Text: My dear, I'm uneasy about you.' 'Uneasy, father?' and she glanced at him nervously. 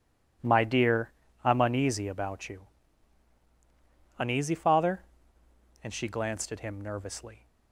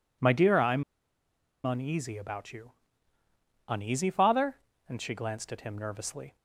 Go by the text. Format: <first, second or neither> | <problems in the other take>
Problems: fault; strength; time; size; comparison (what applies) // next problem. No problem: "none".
first | pauses between "I'm" and "uneasy"; noticeable; at 0.8 s; 0.81 s long